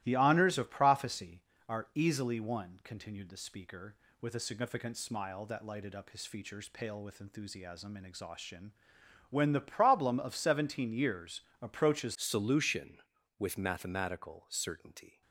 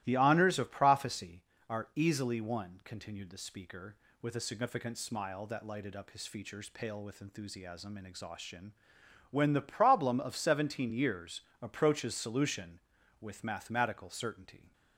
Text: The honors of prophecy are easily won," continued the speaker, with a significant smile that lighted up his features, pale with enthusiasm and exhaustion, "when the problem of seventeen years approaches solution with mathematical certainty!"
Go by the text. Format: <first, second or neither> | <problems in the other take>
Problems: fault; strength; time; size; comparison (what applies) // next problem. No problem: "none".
second | starts louder than the rest; strong; until 1.0 s; 16 dB; strong in the second // pauses between "years" and "approaches"; slight; at 11.4 s; 0.18 s long; slight in the second // changes voice at "solution"; from 12.1 s on; 3.1 s long